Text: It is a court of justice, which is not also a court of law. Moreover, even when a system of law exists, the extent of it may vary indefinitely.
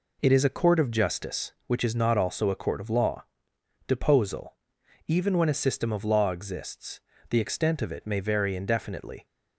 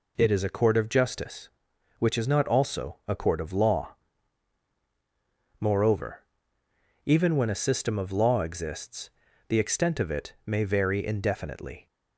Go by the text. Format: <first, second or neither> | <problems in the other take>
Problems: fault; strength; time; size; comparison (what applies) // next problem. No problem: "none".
second | says "Deposal" for "Moreover"; at 3.8 s